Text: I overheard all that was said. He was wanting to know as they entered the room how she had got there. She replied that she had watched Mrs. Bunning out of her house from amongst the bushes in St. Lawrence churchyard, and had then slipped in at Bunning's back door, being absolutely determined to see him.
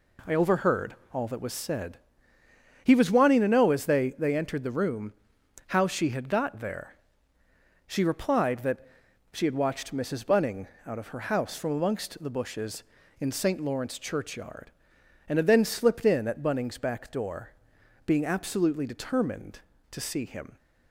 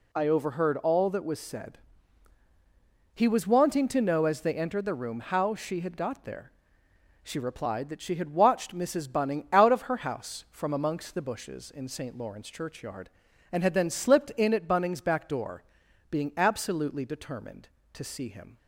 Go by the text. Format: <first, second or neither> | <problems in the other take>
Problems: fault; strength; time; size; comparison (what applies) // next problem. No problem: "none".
second | pauses between "overheard" and "all"; slight; at 0.9 s; 0.18 s long // says "they" twice; at 4.1 s // pauses between "room" and "how"; noticeable; at 5.1 s; 0.56 s long // pauses between "that" and "she"; noticeable; at 8.8 s; 0.46 s long // pauses between "Bunning" and "out"; slight; at 10.6 s; 0.20 s long